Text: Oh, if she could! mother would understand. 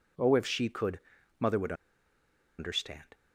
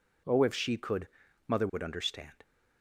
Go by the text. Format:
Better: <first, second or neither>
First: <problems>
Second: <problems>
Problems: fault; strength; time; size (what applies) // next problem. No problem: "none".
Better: second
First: pauses between "would" and "understand"; noticeable; at 1.7 s; 0.85 s long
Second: none